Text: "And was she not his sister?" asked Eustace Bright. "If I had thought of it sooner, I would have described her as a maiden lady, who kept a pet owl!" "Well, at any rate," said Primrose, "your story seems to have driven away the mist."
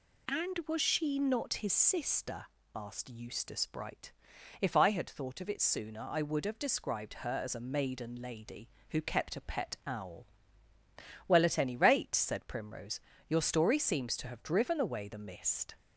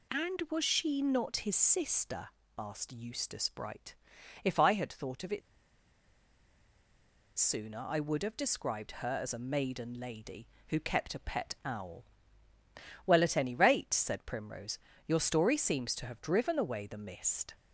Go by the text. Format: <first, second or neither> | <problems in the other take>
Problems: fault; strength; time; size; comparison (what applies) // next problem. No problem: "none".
first | pauses between "it" and "sooner"; strong; at 5.4 s; 1.9 s long